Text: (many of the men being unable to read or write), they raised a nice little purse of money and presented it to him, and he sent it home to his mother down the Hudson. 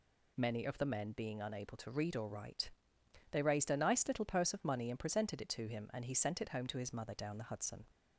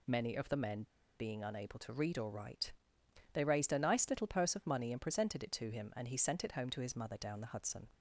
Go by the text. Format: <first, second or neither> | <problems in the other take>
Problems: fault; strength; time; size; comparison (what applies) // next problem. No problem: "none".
first | pauses between "men" and "being"; slight; at 0.8 s; 0.34 s long